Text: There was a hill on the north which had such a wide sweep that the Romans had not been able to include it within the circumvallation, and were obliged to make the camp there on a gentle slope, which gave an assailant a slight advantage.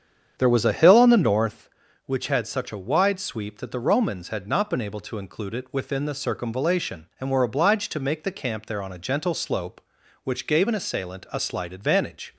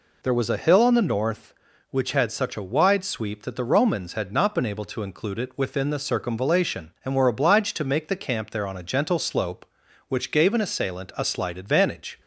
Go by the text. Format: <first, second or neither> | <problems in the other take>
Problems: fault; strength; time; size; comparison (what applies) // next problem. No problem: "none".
second | starts louder than the rest; strong; until 1.6 s; 8 dB